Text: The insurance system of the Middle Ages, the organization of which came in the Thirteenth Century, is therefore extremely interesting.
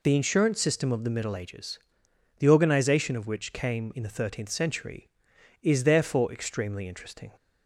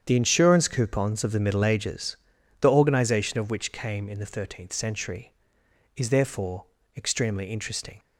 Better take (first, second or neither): first